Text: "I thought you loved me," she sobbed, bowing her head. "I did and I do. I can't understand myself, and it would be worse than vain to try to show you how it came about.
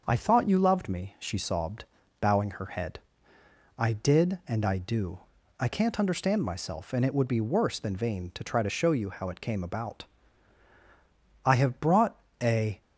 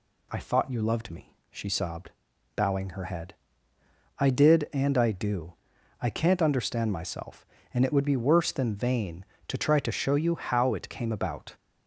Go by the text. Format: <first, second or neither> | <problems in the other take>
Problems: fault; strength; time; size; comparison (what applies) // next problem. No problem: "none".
second | starts louder than the rest; until 1.0 s; 6.5 dB // goes on to say "I have brought a"; from 11.4 s on; 1.3 s long